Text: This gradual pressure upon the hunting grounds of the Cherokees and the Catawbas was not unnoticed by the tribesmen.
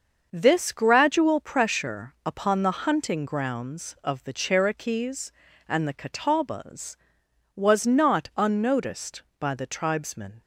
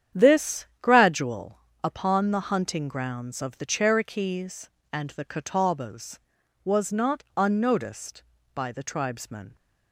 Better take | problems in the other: first | starts louder than the rest; strong; until 1.3 s; 9 dB; also in the first // pauses between "This" and "gradual"; slight; at 0.6 s; 0.16 s long // skips "pressure"; at 1.6 s

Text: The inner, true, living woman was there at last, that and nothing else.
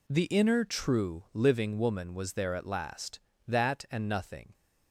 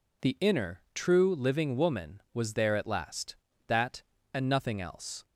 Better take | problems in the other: second | stops before "else"; at 4.5 s

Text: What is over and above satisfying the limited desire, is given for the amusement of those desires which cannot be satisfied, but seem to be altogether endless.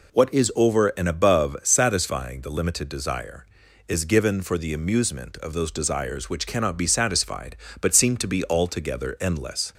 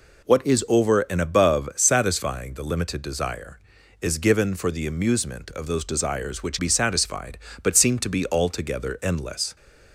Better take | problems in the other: first | skips "cannot"; at 6.5 s

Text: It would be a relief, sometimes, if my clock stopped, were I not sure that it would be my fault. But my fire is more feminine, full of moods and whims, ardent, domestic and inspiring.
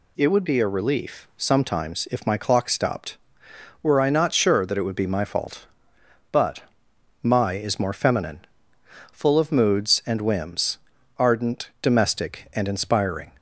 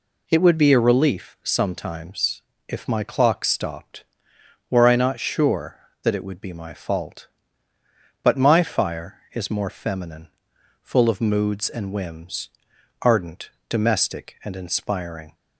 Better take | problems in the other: second | pauses between "But" and "my"; noticeable; at 6.6 s; 0.58 s long // skips "fire"; at 7.5 s

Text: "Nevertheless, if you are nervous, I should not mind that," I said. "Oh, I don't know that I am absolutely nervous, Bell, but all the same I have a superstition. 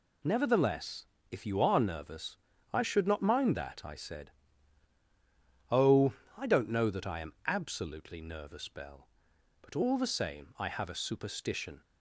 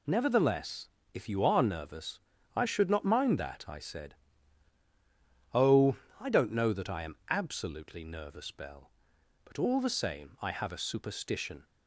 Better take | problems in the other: neither | none

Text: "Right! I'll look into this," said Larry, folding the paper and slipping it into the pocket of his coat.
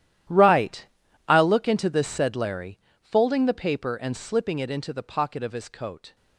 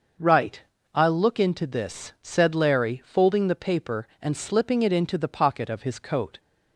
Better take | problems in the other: second | gets quieter; strong; throughout; 17.5 dB // starts louder than the rest; strong; until 1.7 s; 12 dB; also in the second

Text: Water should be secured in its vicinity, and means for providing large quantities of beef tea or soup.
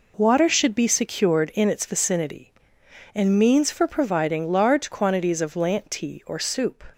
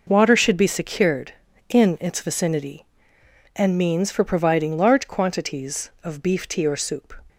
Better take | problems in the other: second | says "lant" for "beef"; at 5.5 s

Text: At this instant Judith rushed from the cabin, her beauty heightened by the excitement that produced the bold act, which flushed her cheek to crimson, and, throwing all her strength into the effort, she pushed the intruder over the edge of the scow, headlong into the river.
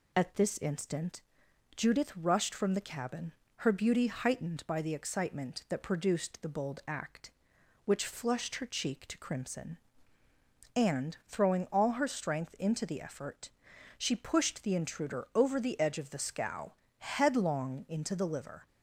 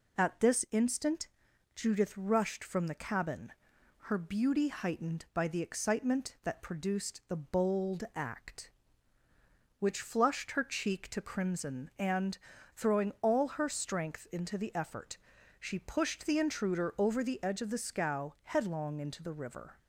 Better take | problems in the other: second | pauses between "instant" and "Judith"; noticeable; at 1.2 s; 0.54 s long; noticeable in the second // says "liver" for "river"; at 18.2 s

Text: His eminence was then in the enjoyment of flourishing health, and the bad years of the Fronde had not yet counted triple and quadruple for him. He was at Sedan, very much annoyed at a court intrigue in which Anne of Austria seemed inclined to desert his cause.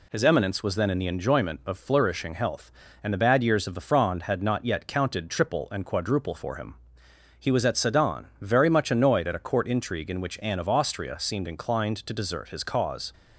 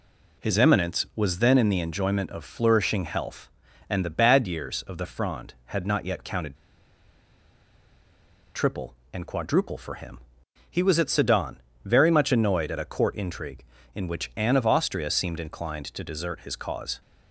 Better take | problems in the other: first | pauses between "counted" and "triple"; strong; at 6.5 s; 1.9 s long

